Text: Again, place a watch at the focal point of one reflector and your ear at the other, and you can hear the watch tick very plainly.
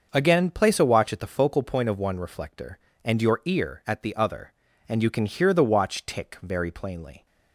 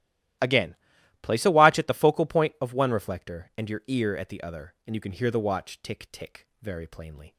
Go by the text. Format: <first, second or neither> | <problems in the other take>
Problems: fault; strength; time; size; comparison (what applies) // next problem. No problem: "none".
first | starts louder than the rest; strong; until 1.8 s; 14.5 dB; also in the first // says "tick" twice; at 6.1 s